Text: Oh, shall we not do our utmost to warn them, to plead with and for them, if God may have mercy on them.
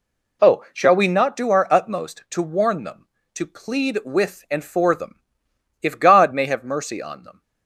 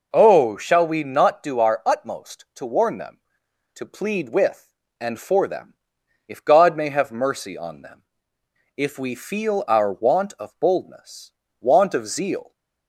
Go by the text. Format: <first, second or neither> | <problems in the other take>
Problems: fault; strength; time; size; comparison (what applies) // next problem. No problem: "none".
first | goes on to say "If we feel our want of boldness want of zeal"; strong; from 8.7 s on; 3.7 s long